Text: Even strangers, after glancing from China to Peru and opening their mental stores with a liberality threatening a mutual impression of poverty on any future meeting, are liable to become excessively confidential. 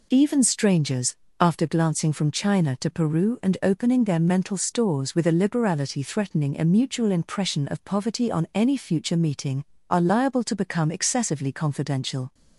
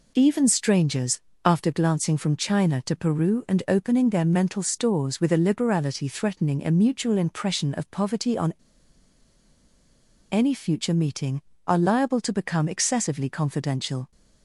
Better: first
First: none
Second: pauses between "on" and "any"; strong; at 8.5 s; 1.7 s long

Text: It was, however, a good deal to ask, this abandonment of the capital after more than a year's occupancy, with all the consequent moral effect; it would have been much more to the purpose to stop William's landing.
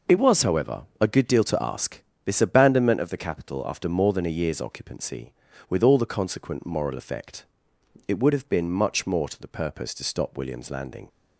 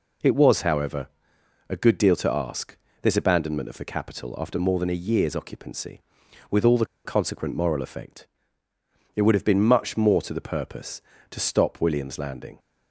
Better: first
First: none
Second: pauses between "the" and "consequent"; slight; at 6.8 s; 0.20 s long

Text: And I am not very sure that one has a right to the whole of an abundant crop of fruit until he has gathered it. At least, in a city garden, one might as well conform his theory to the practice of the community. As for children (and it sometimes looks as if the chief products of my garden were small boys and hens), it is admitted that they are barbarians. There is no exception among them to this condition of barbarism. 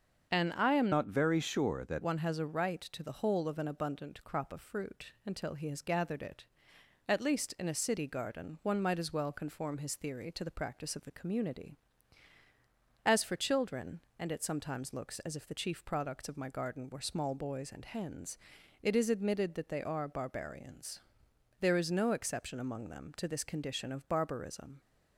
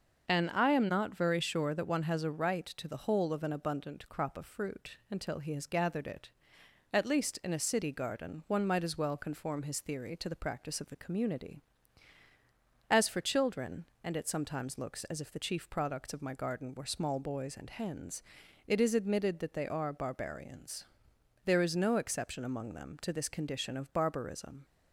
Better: second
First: starts louder than the rest; until 1.3 s; 7 dB // changes voice from "not" to "that"; from 0.9 to 2.0 s; 1.1 s long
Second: starts louder than the rest; until 1.3 s; 6.5 dB

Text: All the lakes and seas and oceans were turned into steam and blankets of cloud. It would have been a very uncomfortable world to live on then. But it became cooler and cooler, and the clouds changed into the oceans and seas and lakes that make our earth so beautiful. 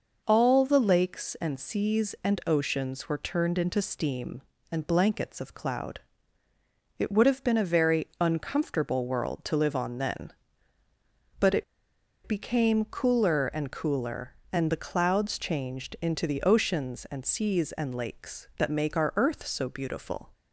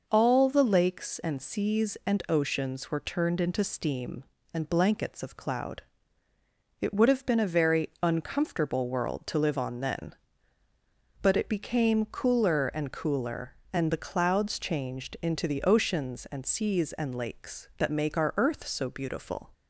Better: second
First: pauses between "it" and "became"; noticeable; at 11.6 s; 0.62 s long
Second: none

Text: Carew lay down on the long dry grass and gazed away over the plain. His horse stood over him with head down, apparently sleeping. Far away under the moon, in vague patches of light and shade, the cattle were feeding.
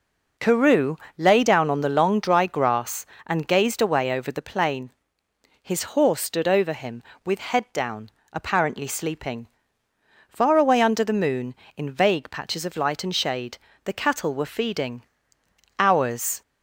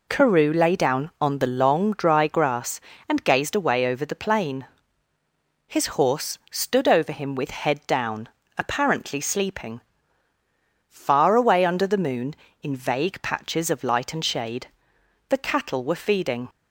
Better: second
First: pauses between "Carew" and "lay"; slight; at 0.9 s; 0.22 s long // goes on to say "Hours"; noticeable; from 15.7 s on; 0.62 s long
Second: none

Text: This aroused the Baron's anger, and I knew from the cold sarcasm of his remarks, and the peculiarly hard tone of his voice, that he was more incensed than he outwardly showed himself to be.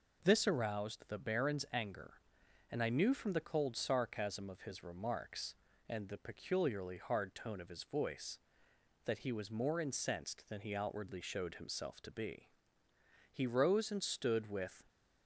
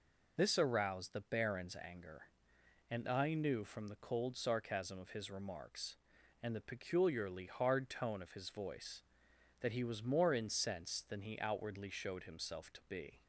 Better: second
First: goes on to say "He rose and stood with"; from 13.3 s on; 1.5 s long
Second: none

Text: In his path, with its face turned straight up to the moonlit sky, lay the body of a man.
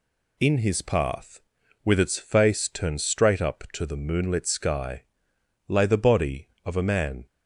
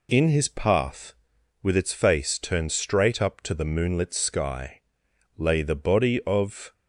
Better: first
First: none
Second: stops before "a man"; at 6.7 s

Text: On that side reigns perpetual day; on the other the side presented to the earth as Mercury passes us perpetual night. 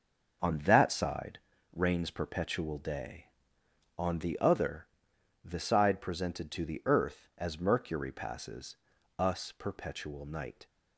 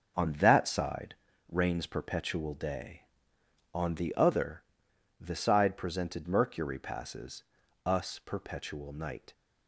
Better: first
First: starts louder than the rest; until 1.8 s; 6.5 dB // pauses between "side" and "reigns"; slight; at 1.3 s; 0.34 s long // pauses between "other" and "the"; noticeable; at 4.8 s; 0.56 s long // pauses between "passes" and "us"; at 8.7 s; 0.40 s long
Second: starts louder than the rest; until 1.5 s; 6.5 dB // pauses between "side" and "reigns"; slight; at 1.1 s; 0.34 s long // pauses between "other" and "the"; noticeable; at 4.6 s; 0.56 s long // skips "to the earth as"; at 6.2 s // pauses between "passes" and "us"; at 7.4 s; 0.40 s long

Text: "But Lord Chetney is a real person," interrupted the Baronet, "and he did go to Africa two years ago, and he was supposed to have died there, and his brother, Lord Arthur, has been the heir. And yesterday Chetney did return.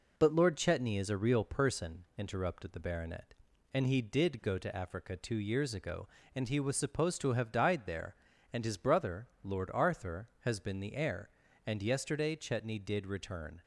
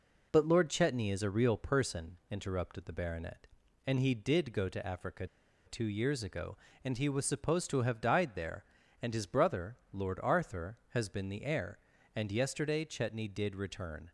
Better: first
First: none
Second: pauses between "Africa" and "two"; at 5.2 s; 0.41 s long

